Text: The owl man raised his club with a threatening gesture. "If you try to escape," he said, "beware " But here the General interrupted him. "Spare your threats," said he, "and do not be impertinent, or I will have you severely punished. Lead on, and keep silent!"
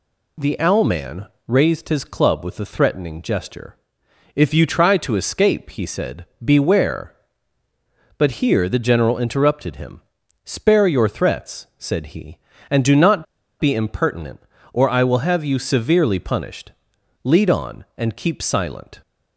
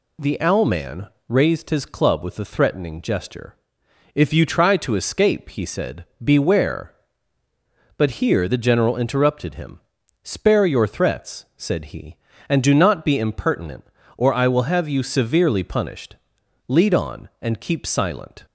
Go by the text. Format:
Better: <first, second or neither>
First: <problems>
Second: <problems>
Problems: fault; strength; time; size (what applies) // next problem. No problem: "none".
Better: second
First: pauses between "man" and "raised"; slight; at 1.2 s; 0.22 s long // pauses between "not" and "be"; slight; at 13.2 s; 0.35 s long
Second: pauses between "man" and "raised"; slight; at 1.0 s; 0.22 s long